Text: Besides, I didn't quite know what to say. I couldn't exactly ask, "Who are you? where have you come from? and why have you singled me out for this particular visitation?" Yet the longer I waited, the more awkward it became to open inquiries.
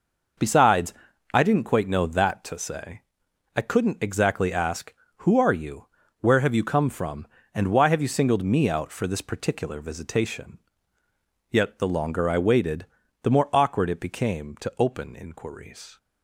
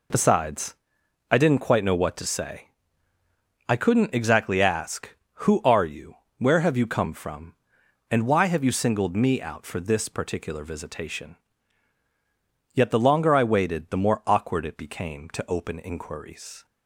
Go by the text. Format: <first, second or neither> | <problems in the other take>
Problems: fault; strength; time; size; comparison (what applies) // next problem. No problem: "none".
second | says "that" for "what"; at 2.0 s